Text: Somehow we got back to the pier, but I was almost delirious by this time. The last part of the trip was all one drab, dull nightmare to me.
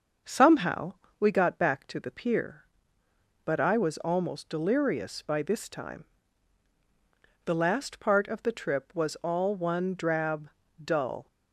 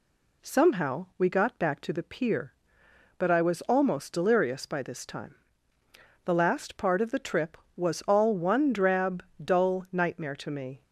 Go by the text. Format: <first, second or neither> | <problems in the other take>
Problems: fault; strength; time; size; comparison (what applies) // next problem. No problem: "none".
second | starts louder than the rest; until 1.4 s; 6.5 dB // pauses between "Somehow" and "we"; slight; at 0.9 s; 0.24 s long // stops before "nightmare to me"; at 11.2 s